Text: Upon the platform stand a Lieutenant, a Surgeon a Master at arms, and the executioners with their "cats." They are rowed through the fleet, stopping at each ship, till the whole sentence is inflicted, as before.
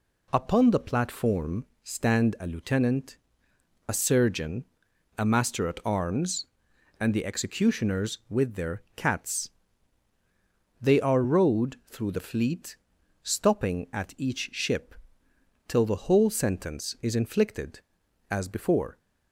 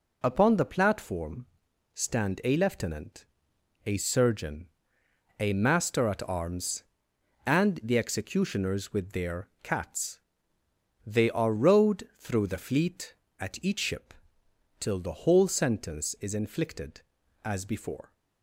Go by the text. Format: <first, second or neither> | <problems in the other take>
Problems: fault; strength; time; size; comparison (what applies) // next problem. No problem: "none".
first | pauses between "platform" and "stand"; noticeable; at 1.4 s; 0.48 s long; slight in the first // pauses between "Surgeon" and "a"; noticeable; at 4.6 s; 0.72 s long; noticeable in the first // skips "stopping"; at 13.2 s